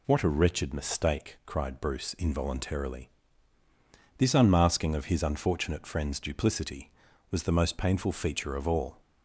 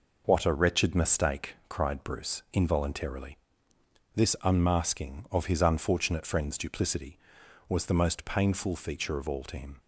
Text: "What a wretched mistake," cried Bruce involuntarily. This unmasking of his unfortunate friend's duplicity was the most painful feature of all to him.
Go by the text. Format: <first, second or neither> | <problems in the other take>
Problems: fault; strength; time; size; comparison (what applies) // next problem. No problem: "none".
second | stops before "to him"; at 9.0 s